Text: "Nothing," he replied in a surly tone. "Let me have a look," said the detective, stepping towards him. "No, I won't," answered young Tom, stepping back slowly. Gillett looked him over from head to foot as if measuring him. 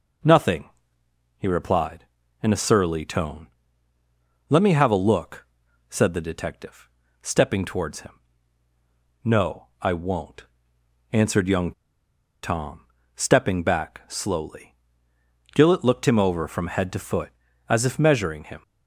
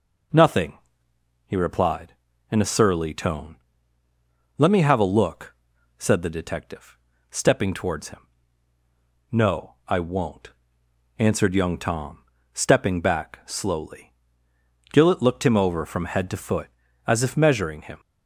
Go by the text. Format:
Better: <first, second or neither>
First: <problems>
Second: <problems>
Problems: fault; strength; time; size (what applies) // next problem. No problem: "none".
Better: second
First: pauses between "young" and "Tom"; noticeable; at 11.7 s; 0.71 s long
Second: none